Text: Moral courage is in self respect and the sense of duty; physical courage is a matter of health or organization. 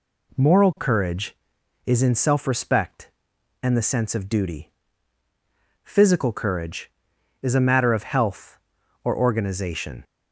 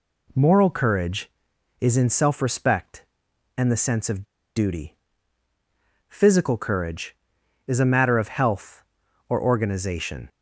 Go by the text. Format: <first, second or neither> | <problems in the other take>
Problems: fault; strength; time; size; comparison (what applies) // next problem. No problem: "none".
first | pauses between "of" and "duty"; slight; at 4.2 s; 0.33 s long